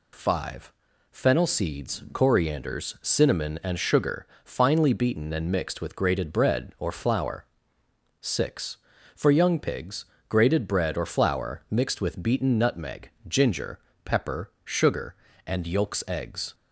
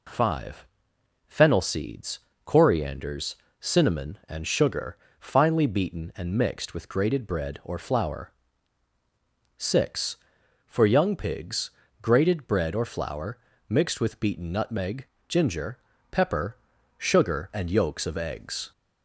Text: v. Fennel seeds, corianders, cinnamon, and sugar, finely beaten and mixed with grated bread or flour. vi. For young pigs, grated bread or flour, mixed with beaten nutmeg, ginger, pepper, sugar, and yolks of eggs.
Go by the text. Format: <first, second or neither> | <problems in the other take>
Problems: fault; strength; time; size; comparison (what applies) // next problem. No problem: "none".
second | skips "of"; at 16.0 s